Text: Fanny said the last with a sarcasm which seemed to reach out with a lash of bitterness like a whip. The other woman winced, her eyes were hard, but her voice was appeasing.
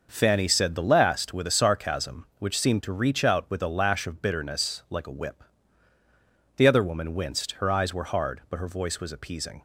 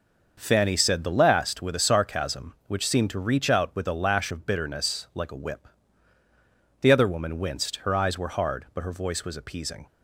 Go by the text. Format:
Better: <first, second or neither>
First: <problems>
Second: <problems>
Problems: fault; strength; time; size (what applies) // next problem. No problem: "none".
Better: neither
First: none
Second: none